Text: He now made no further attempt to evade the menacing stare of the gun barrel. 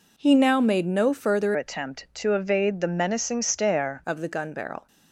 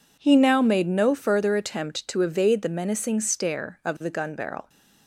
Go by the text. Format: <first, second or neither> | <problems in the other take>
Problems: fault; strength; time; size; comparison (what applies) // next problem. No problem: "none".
second | changes voice from "attempt" to "stare"; from 1.5 to 4.0 s; 2.5 s long